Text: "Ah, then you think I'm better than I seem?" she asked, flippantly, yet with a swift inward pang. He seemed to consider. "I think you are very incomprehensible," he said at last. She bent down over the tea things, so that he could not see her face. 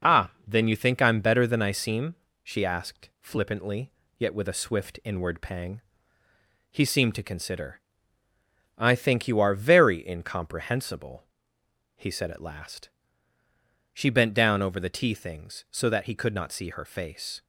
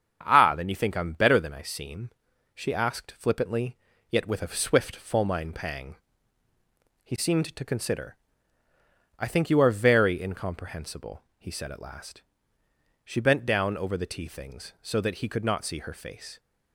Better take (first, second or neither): first